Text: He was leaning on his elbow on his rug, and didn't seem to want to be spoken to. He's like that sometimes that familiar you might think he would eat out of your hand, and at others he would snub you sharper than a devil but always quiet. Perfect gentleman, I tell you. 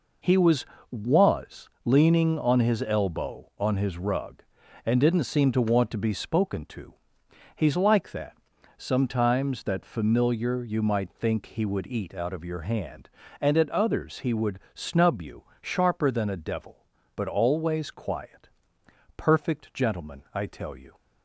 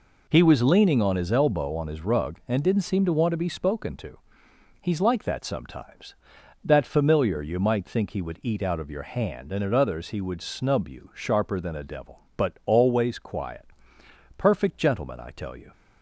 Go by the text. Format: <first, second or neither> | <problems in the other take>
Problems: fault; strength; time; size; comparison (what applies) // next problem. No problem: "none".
second | says "was" twice; at 0.8 s // pauses between "that" and "sometimes"; at 8.3 s; 0.40 s long // pauses between "you" and "sharper"; slight; at 15.4 s; 0.18 s long